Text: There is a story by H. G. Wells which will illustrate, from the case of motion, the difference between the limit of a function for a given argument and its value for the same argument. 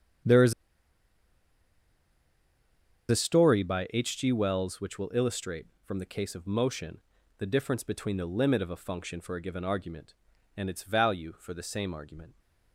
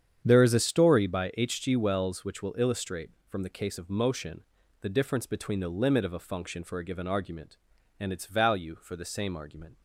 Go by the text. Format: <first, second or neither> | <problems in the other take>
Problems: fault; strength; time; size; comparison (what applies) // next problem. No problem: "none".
second | starts louder than the rest; strong; until 3.8 s; 8 dB; strong in the second // pauses between "is" and "a"; strong; at 0.5 s; 2.5 s long